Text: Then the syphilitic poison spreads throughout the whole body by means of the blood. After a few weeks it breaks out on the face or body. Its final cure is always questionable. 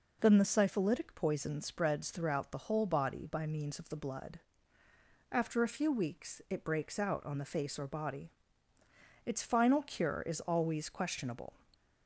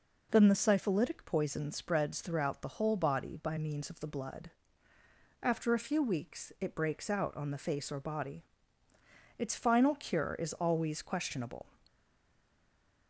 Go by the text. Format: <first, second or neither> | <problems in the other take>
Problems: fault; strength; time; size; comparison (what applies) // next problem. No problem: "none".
first | stays silent after the last word; noticeable; from 11.8 s on; 1.2 s long